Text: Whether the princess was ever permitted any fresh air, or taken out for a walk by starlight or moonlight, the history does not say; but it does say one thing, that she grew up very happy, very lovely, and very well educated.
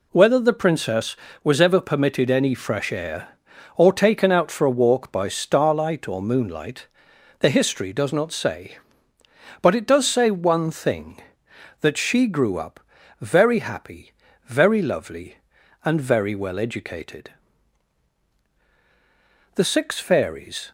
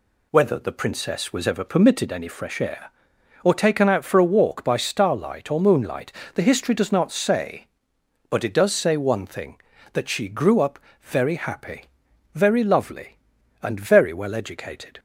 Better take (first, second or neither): second